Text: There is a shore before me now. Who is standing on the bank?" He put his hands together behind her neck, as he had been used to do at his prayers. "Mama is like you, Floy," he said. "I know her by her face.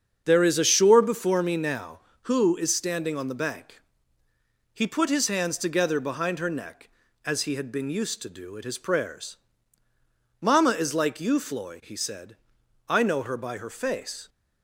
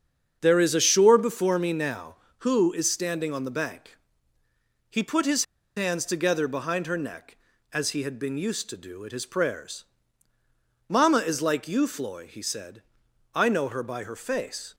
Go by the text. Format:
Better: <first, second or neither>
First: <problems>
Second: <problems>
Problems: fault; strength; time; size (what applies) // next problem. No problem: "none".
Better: first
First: starts louder than the rest; strong; until 1.2 s; 7 dB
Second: starts louder than the rest; strong; until 1.4 s; 7 dB // pauses between "his" and "hands"; slight; at 5.4 s; 0.31 s long